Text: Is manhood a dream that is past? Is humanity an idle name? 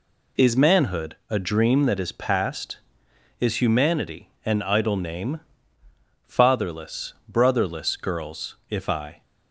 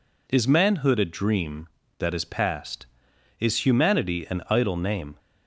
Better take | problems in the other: second | pauses between "humanity" and "an"; slight; at 4.2 s; 0.16 s long // goes on to say "Fatherless brotherless girls if I"; strong; from 6.2 s on; 2.9 s long

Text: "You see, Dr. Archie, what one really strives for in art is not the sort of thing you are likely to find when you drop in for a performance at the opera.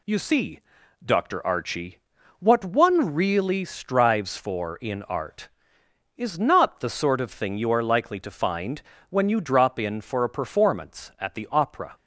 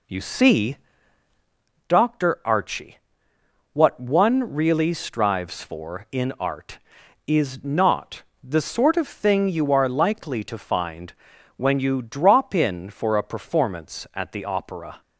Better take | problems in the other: first | starts louder than the rest; slight; until 1.9 s; 3 dB // pauses between "not" and "the"; slight; at 8.2 s; 0.20 s long // pauses between "find" and "when"; at 11.1 s; 0.44 s long; slight in the first

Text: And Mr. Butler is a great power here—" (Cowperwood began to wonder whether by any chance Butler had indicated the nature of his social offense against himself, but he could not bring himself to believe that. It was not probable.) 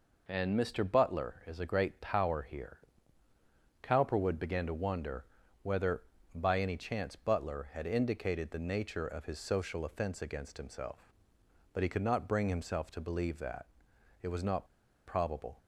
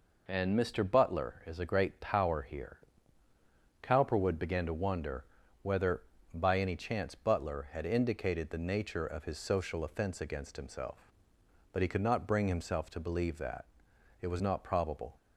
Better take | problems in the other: second | pauses between "wonder" and "whether"; slight; at 5.2 s; 0.36 s long; slight in the second // pauses between "not" and "probable"; at 14.6 s; 0.43 s long

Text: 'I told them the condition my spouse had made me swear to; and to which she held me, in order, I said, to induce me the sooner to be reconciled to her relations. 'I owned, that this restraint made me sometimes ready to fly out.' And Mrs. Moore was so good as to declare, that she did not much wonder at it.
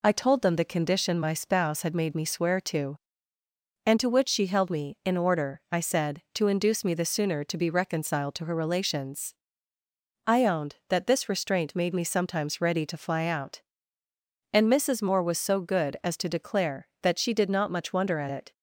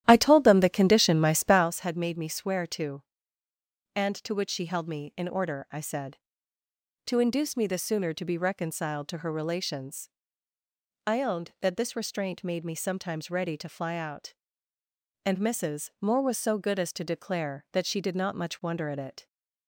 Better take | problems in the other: first | starts louder than the rest; strong; until 1.7 s; 12 dB

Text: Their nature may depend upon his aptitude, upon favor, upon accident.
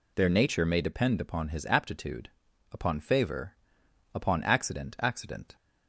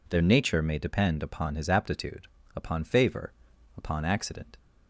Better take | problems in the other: second | says "accident" twice; at 4.9 s

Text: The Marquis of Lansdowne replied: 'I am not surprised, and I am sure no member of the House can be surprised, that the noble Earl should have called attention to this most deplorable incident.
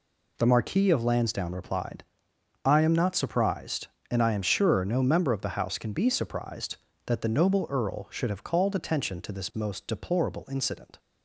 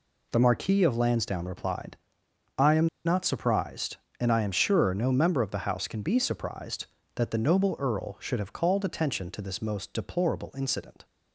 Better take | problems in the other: first | pauses between "am" and "not"; slight; at 2.8 s; 0.19 s long

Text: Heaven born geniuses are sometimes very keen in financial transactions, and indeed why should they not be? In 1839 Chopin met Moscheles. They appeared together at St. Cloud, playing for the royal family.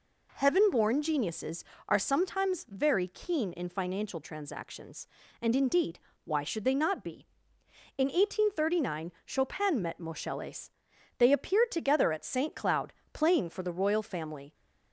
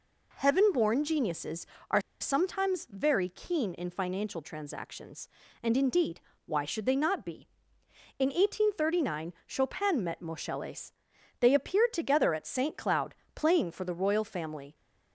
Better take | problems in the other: first | pauses between "are" and "sometimes"; slight; at 1.9 s; 0.20 s long // pauses between "indeed" and "why"; slight; at 6.2 s; 0.24 s long; slight in the first

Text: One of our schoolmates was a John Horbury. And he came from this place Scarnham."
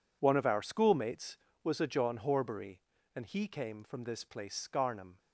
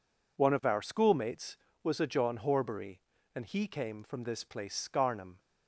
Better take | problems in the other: second | gets quieter; strong; throughout; 15.5 dB

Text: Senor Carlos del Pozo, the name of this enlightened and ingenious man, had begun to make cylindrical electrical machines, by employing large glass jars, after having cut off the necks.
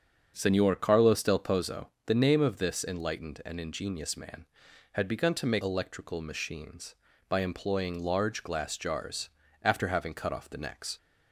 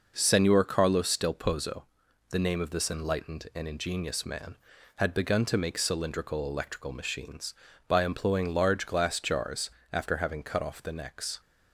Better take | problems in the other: second | starts louder than the rest; until 1.3 s; 7 dB // skips "cylindrical"; at 5.6 s

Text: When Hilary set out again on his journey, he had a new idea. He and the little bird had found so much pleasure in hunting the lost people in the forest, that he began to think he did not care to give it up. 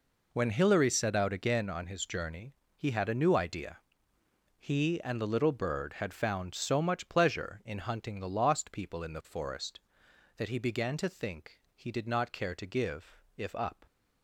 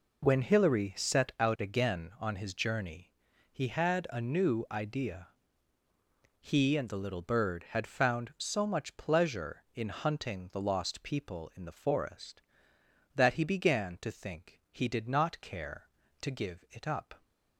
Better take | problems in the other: second | says "if" for "it"; at 13.3 s

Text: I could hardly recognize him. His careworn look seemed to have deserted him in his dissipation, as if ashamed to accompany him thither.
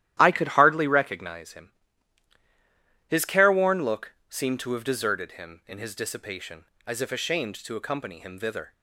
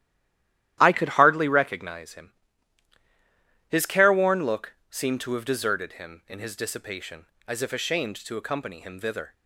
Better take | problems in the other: first | stays silent before the first word; slight; until 0.7 s; 0.7 s long // starts louder than the rest; strong; until 1.8 s; 12.5 dB; strong in the first

